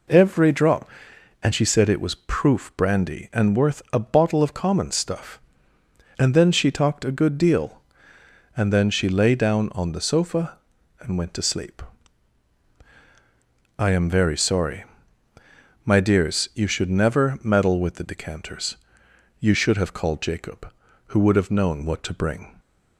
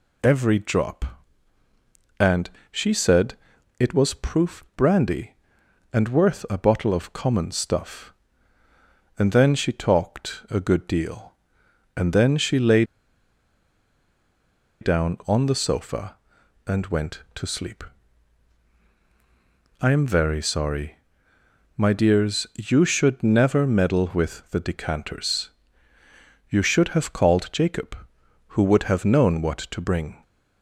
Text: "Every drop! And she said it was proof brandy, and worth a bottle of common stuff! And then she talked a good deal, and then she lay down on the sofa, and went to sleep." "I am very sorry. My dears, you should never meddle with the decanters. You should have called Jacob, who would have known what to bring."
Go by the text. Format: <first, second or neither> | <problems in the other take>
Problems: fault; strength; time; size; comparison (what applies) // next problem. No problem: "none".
first | pauses between "And" and "she"; slight; at 2.4 s; 0.20 s long // pauses between "said" and "it"; at 3.3 s; 0.42 s long // pauses between "lay" and "down"; strong; at 12.8 s; 1.9 s long